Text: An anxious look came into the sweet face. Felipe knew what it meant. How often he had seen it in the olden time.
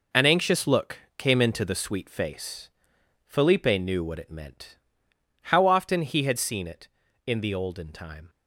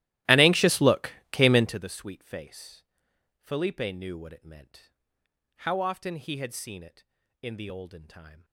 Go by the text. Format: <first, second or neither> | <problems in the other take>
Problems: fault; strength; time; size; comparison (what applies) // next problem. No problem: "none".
first | starts louder than the rest; strong; until 1.8 s; 16 dB // pauses between "look" and "came"; slight; at 1.1 s; 0.18 s long; slight in the first